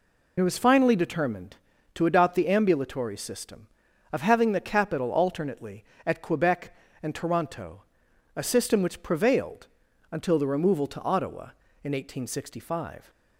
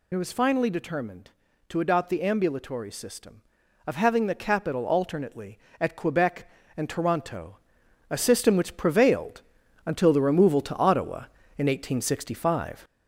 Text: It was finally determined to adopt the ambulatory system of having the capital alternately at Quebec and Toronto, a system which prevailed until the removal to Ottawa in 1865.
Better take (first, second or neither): first